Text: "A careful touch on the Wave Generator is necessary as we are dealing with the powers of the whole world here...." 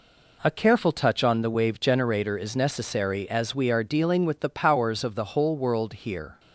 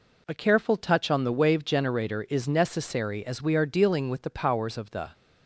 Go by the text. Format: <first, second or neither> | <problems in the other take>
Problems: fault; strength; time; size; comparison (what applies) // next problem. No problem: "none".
first | stops before "whole world here"; at 5.1 s